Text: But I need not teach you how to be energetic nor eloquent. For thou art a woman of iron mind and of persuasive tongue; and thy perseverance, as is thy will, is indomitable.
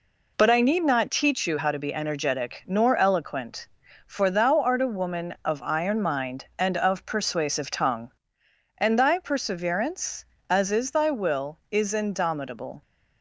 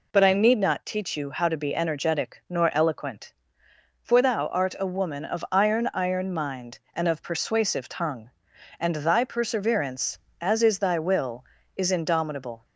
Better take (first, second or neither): first